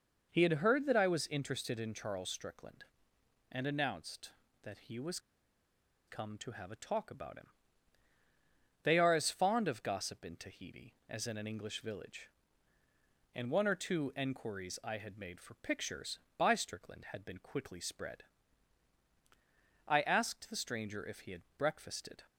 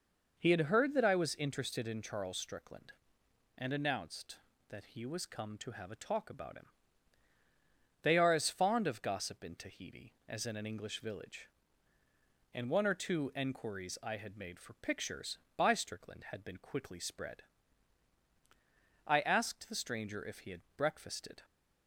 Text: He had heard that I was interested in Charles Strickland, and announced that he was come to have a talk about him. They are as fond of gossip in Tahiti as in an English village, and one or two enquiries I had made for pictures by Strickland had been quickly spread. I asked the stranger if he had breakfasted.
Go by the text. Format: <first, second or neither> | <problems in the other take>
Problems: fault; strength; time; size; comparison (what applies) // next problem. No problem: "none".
second | pauses between "was" and "come"; noticeable; at 5.1 s; 0.89 s long